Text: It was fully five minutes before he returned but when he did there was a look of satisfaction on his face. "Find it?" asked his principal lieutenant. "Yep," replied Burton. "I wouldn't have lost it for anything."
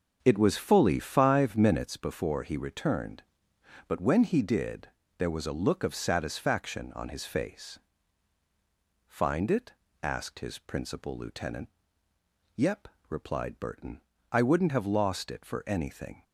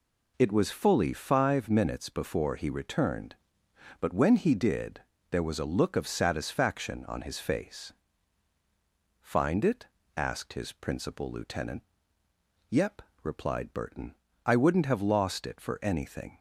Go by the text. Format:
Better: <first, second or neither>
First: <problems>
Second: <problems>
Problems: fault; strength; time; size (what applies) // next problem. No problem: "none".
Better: second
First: starts louder than the rest; until 2.1 s; 6.5 dB // pauses between "did" and "there"; slight; at 4.8 s; 0.30 s long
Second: pauses between "did" and "there"; slight; at 5.0 s; 0.30 s long